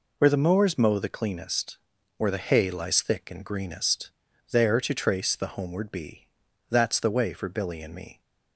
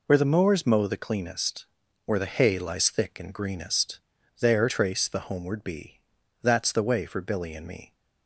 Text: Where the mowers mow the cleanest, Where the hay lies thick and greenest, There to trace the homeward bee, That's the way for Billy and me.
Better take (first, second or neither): first